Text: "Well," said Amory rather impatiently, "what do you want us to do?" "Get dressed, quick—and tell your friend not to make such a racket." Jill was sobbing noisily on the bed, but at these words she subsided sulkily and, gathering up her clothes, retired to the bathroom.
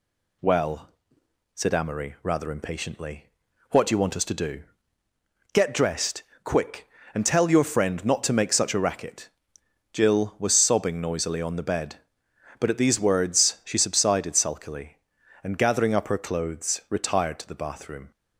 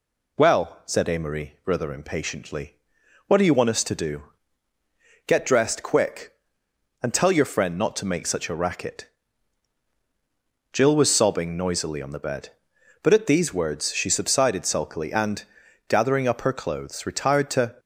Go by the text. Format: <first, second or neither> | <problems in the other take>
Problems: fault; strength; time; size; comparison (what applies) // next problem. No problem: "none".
first | stops before "the bathroom"; at 17.7 s